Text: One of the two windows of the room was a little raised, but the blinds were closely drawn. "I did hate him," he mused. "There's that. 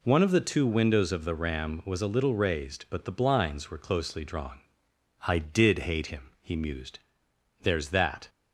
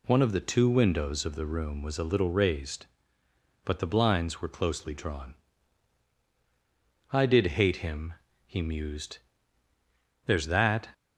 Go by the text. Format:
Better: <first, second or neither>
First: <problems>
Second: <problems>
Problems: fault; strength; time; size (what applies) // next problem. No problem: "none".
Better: second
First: says "ram" for "room"; at 1.3 s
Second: none